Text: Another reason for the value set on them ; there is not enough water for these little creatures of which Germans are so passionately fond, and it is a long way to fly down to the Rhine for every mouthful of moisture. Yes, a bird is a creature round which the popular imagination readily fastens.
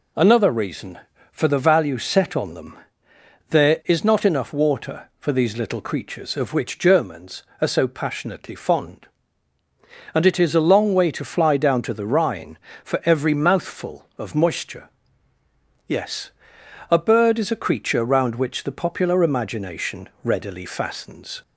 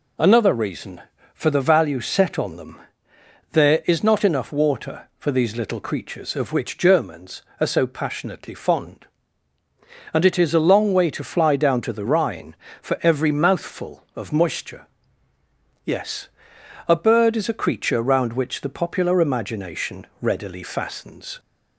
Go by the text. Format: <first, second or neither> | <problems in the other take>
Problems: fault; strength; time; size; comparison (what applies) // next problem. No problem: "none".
neither | pauses between "imagination" and "readily"; slight; the same in both